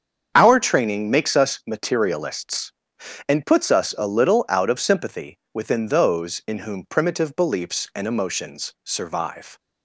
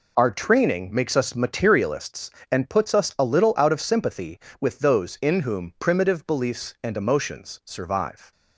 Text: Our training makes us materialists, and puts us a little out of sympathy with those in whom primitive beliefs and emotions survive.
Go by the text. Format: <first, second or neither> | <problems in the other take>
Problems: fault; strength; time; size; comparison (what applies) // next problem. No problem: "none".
second | starts louder than the rest; until 1.3 s; 7 dB // says "within" for "with"; at 5.5 s